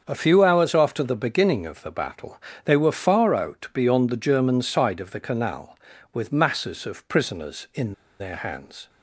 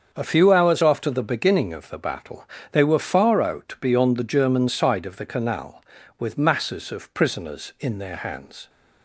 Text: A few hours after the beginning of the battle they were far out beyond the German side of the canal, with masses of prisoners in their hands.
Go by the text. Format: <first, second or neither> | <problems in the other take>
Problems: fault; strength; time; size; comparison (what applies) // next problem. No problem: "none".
second | starts louder than the rest; until 1.0 s; 7 dB; also in the second // pauses between "battle" and "they"; slight; at 2.3 s; 0.28 s long; slight in the second // pauses between "in" and "their"; slight; at 7.9 s; 0.26 s long